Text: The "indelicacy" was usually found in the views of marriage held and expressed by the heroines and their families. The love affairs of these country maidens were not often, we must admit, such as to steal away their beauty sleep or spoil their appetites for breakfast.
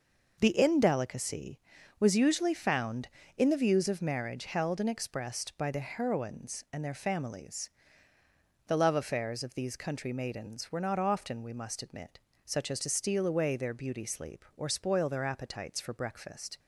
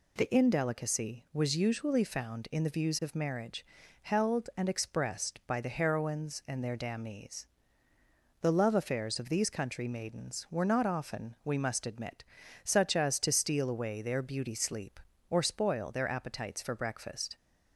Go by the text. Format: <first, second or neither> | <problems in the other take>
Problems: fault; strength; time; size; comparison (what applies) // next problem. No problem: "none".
first | pauses between "marriage" and "held"; at 3.6 s; 0.38 s long // says "damnees" for "families"; at 6.7 s